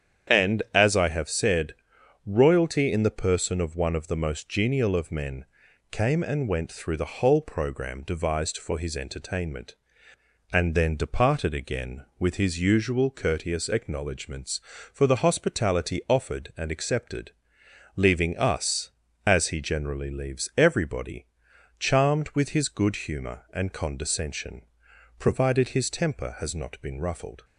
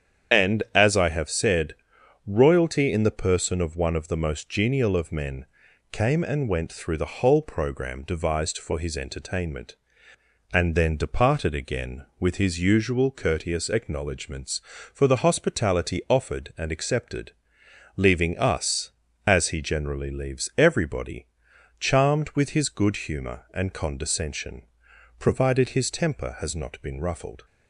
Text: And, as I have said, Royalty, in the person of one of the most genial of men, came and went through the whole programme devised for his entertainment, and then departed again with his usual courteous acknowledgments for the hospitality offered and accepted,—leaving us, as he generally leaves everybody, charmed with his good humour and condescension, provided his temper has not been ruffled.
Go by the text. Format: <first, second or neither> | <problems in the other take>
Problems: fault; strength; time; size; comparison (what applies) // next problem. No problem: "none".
first | loses the start of "And"; at 0.3 s; 35 ms // starts louder than the rest; strong; until 1.4 s; 8.5 dB; strong in the first